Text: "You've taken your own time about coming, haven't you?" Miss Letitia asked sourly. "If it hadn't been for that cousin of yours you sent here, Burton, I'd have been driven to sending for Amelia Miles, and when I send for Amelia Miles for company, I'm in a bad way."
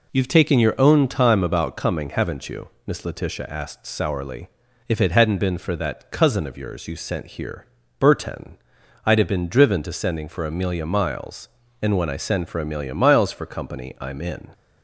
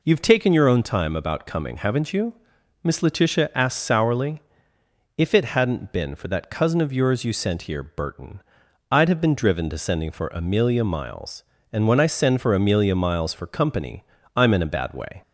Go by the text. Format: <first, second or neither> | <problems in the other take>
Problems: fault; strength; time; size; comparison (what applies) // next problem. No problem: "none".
second | stops before "a bad way"; at 14.5 s